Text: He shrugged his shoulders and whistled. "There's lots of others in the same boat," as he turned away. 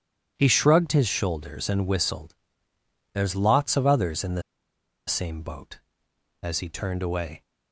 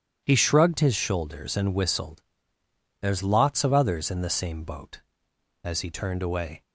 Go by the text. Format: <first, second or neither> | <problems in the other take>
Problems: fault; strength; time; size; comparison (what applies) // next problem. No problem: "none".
second | pauses between "the" and "same"; noticeable; at 4.4 s; 0.66 s long